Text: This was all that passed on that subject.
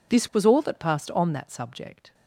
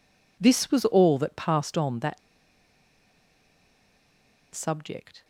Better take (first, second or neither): first